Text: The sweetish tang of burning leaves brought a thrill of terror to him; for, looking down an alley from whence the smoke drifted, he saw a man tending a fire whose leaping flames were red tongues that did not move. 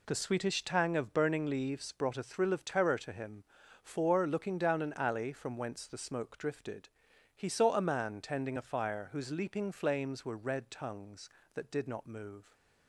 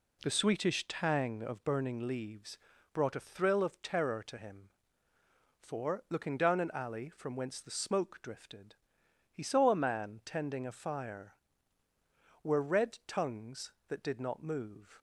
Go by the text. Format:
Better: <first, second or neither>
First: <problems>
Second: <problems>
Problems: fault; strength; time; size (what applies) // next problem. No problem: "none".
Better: first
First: none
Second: pauses between "leaves" and "brought"; slight; at 2.5 s; 0.34 s long // skips "whose leaping flames"; at 11.8 s